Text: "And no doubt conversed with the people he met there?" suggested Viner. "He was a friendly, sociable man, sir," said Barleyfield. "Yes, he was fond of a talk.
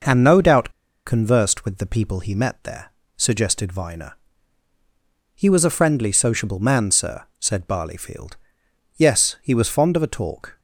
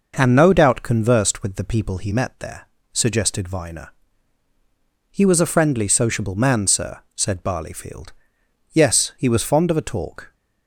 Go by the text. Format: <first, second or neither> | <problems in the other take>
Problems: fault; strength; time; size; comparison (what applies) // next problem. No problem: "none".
second | pauses between "doubt" and "conversed"; slight; at 0.7 s; 0.35 s long